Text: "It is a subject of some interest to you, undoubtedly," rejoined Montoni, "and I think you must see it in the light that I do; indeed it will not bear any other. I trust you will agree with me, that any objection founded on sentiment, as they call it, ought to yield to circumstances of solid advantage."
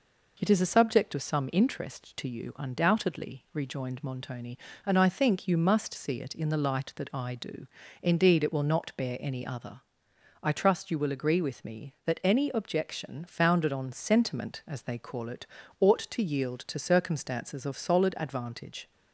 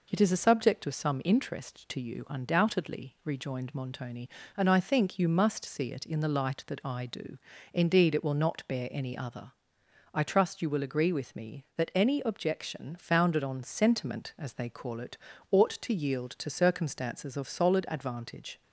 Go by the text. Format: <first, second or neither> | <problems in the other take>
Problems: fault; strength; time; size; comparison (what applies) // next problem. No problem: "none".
neither | none